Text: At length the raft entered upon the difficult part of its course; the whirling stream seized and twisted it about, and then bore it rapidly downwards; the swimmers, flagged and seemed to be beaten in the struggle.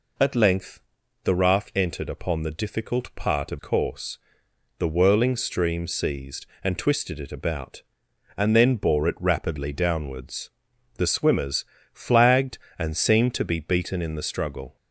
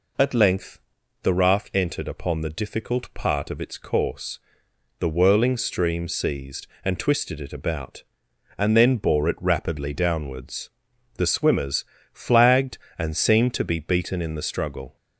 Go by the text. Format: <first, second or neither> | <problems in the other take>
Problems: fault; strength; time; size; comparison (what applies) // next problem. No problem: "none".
second | pauses between "length" and "the"; at 0.8 s; 0.44 s long; also in the second // skips "its"; at 3.5 s